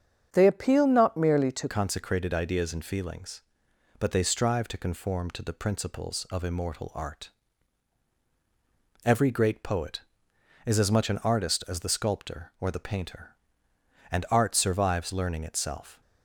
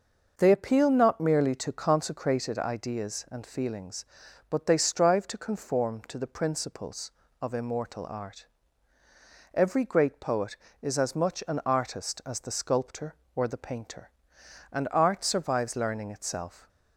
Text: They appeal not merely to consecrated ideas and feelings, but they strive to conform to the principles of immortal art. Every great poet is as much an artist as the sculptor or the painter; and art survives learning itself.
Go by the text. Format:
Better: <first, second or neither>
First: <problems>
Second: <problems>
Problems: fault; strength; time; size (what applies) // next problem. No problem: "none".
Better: second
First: starts louder than the rest; strong; until 1.3 s; 7.5 dB // changes voice at "consecrated"; from 1.6 s on; 14.4 s long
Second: none